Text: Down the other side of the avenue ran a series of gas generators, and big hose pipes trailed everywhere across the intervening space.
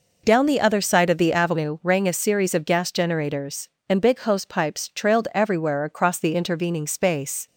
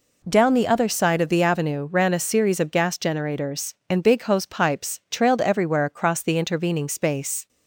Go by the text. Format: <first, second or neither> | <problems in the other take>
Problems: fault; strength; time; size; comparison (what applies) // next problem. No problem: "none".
second | says "rang" for "ran"; at 1.8 s